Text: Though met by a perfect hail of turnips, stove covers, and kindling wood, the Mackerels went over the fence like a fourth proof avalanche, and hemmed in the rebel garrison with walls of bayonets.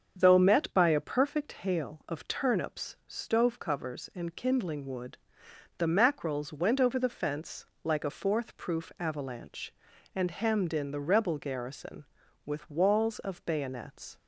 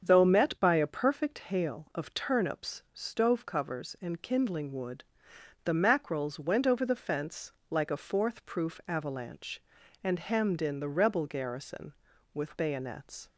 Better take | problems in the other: first | starts louder than the rest; until 1.0 s; 7 dB; also in the first // pauses between "fence" and "like"; slight; at 7.5 s; 0.16 s long; slight in the first // skips "walls of"; at 12.5 s

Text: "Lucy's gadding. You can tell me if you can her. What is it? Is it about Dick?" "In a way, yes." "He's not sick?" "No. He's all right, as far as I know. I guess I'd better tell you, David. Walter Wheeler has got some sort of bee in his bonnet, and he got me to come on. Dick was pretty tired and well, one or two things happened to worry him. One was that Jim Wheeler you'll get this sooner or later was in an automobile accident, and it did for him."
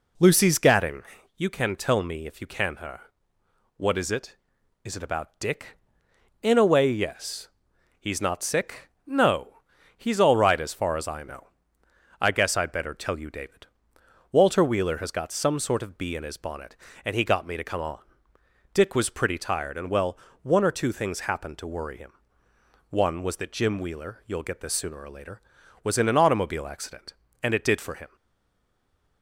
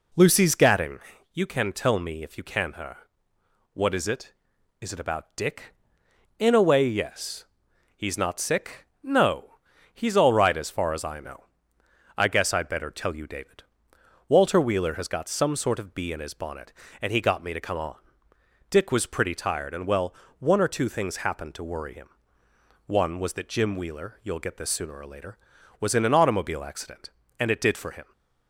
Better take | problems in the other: second | stays silent after the last word; from 28.1 s on; 1.1 s long

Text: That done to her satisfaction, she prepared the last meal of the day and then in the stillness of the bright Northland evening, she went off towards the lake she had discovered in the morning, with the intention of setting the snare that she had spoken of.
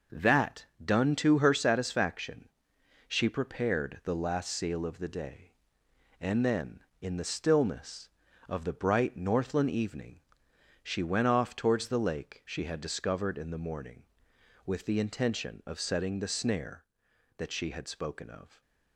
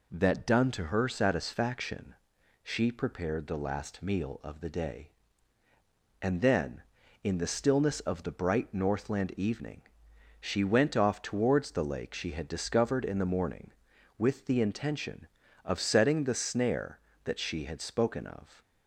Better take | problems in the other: second | starts louder than the rest; noticeable; until 1.3 s; 6 dB // pauses between "That" and "done"; slight; at 0.6 s; 0.20 s long // says "seal" for "meal"; at 4.5 s

